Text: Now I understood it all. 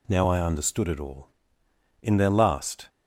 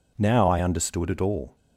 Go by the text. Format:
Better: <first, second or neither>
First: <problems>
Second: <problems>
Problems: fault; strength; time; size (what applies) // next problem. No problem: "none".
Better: second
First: goes on to say "In their last"; noticeable; from 2.0 s on; 0.86 s long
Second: none